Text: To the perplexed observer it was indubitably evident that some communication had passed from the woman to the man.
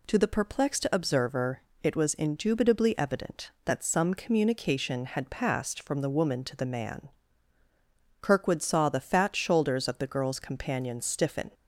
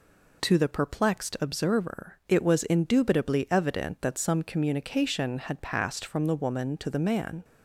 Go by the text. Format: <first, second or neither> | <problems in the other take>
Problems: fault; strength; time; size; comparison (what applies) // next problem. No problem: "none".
second | pauses between "observer" and "it"; slight; at 1.6 s; 0.22 s long // goes on to say "Kirkwood saw the fat shoulders of the girl's companion stiffen"; strong; from 8.1 s on; 3.3 s long